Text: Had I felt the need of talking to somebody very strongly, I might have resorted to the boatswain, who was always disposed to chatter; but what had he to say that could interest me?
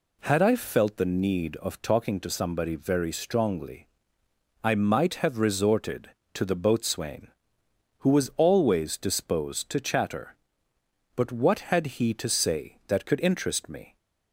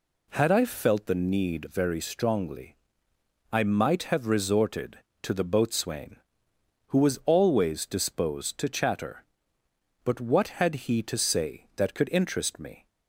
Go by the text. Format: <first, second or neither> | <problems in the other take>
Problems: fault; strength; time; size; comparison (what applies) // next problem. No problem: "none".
first | skips "of talking to somebody"; at 1.6 s